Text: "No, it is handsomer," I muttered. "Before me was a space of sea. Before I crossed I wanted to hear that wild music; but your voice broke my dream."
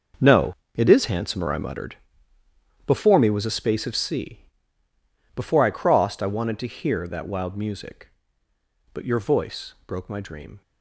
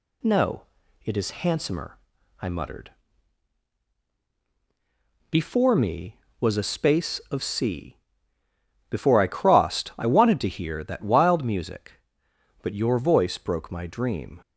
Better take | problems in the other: second | gets quieter; strong; throughout; 13 dB

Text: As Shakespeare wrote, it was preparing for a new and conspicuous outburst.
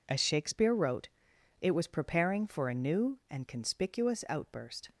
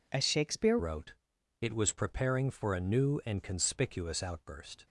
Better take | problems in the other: first | changes voice at "wrote"; from 0.7 s on; 4.1 s long

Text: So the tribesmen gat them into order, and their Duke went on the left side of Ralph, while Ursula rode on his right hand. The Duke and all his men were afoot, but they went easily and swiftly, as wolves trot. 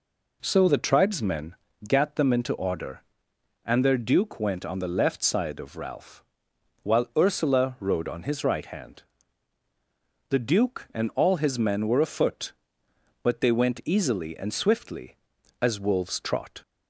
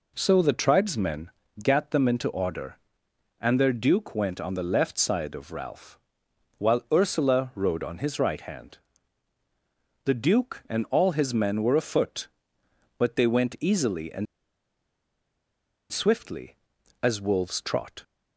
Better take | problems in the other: first | pauses between "tribesmen" and "gat"; slight; at 1.3 s; 0.30 s long; slight in the first // pauses between "and" and "swiftly"; strong; at 14.2 s; 1.6 s long

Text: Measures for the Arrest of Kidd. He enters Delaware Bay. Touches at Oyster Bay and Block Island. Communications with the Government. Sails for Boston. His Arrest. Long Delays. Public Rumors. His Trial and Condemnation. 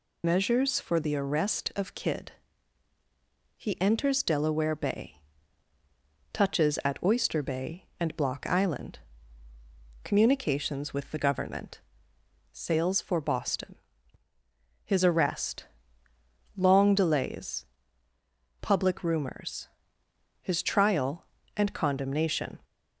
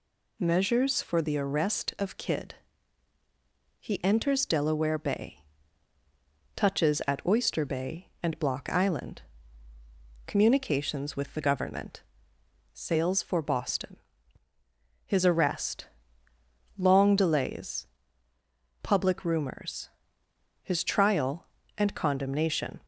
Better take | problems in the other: second | loses the start of "Measures"; at 0.2 s; 65 ms

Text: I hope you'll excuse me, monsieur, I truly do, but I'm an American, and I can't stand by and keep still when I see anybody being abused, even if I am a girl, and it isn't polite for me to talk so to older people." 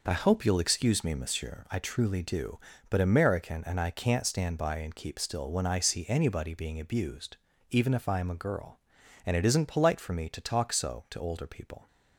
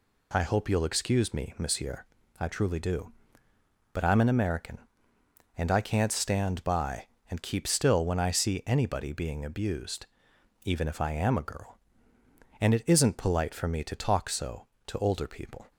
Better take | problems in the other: second | skips "I'm an"; at 3.0 s

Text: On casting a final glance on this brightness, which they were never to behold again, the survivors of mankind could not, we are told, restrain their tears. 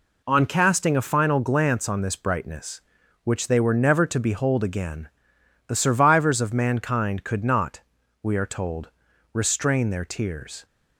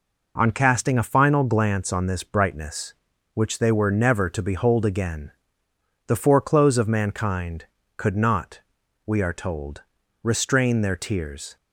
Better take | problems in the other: first | says "foreclose" for "survivors"; at 6.1 s

